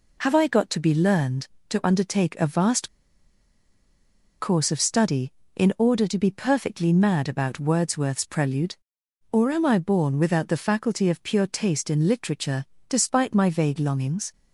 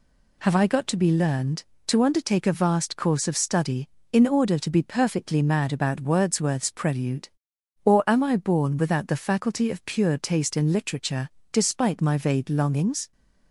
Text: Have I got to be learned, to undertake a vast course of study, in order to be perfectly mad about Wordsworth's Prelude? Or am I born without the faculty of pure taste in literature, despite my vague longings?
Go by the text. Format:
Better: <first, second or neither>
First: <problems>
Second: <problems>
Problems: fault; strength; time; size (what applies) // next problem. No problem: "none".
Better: second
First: pauses between "vast" and "course"; strong; at 2.8 s; 1.5 s long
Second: none